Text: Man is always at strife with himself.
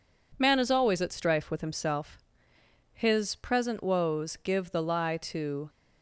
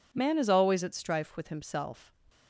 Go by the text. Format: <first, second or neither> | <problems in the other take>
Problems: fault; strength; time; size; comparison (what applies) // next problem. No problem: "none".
second | goes on to say "His present woes give the lie to"; strong; from 2.9 s on; 2.7 s long